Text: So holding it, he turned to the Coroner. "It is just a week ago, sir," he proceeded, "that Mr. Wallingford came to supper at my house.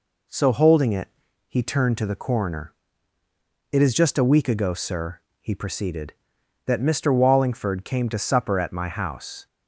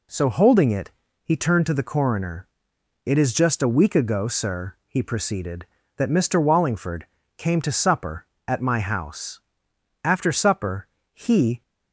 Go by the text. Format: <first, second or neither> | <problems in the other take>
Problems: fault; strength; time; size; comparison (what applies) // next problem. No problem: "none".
first | pauses between "Wallingford" and "came"; slight; at 7.0 s; 0.32 s long // goes on to say "After supper he"; from 10.0 s on; 1.5 s long